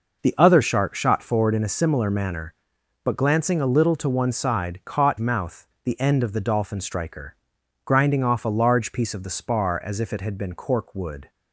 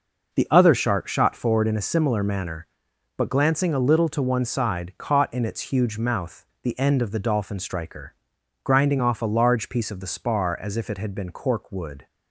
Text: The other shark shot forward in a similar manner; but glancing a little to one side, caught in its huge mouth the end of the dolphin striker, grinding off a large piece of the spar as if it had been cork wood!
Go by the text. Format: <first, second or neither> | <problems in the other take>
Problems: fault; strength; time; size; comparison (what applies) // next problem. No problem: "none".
second | skips "in its huge"; at 5.1 s // pauses between "mouth" and "the"; slight; at 5.6 s; 0.16 s long; slight in the second